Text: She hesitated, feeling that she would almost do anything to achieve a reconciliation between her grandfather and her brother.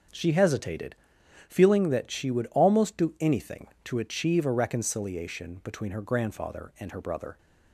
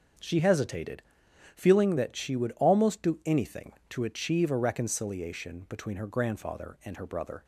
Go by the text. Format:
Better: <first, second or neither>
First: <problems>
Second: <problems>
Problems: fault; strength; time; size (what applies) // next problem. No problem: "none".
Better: neither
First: starts louder than the rest; until 1.6 s; 6.5 dB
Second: starts louder than the rest; until 1.7 s; 6.5 dB